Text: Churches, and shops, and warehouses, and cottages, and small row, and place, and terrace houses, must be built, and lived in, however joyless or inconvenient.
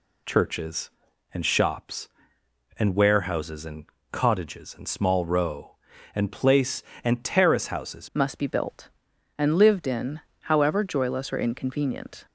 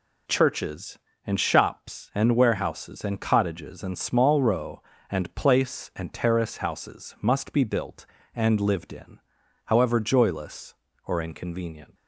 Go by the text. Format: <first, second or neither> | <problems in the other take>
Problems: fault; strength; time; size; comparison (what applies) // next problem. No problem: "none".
second | pauses between "and" and "cottages"; slight; at 3.8 s; 0.26 s long // changes voice at "must"; from 8.1 s on; 4.1 s long